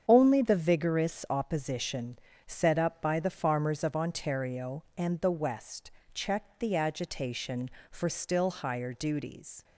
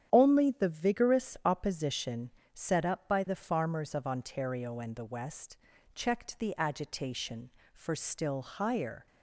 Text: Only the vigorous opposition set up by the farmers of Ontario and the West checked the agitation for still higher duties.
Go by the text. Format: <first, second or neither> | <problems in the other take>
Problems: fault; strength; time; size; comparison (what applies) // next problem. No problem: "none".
first | starts louder than the rest; strong; until 1.1 s; 9.5 dB; strong in the first // pauses between "opposition" and "set"; slight; at 2.2 s; 0.22 s long; slight in the first // pauses between "West" and "checked"; at 5.5 s; 0.38 s long; slight in the first // stops before "duties"; at 9.0 s